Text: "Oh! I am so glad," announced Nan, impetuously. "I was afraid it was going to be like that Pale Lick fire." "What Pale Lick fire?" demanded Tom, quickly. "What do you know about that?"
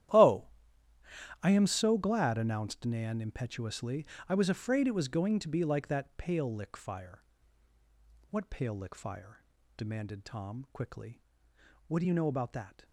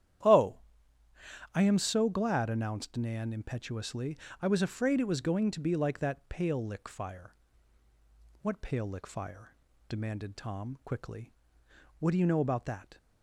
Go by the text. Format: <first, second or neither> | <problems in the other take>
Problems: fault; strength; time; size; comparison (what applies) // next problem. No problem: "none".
second | gets quieter; strong; throughout; 16 dB // starts louder than the rest; strong; until 2.1 s; 12 dB; strong in the second